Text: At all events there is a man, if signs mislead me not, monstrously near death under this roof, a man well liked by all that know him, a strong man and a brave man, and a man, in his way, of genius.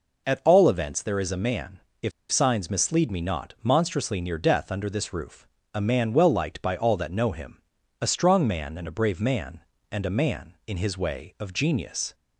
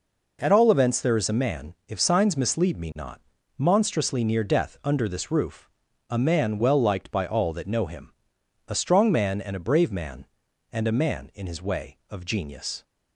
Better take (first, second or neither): second